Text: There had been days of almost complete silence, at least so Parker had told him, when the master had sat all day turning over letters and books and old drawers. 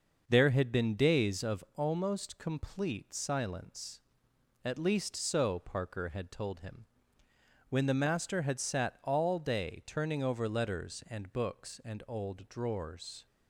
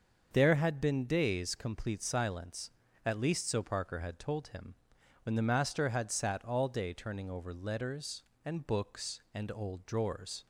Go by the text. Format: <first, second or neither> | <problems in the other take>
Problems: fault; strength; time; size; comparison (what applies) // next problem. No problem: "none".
first | starts louder than the rest; until 1.3 s; 6.5 dB; noticeable in the first // skips "of almost"; at 1.5 s